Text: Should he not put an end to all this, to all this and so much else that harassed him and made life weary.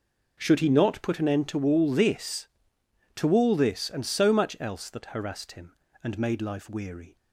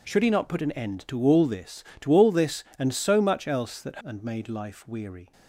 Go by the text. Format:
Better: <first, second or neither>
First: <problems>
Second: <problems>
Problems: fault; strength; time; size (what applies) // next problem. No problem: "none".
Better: first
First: none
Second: skips "harassed him"; at 4.0 s